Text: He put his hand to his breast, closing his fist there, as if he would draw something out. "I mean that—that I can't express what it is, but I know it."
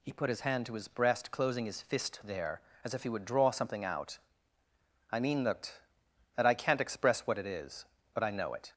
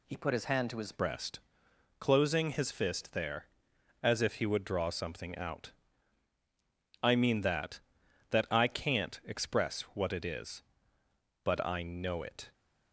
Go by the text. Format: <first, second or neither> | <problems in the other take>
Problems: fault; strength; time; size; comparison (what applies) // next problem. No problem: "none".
first | changes voice at "breast"; from 0.9 s on; 11.6 s long // pauses between "express" and "what"; slight; at 9.8 s; 0.16 s long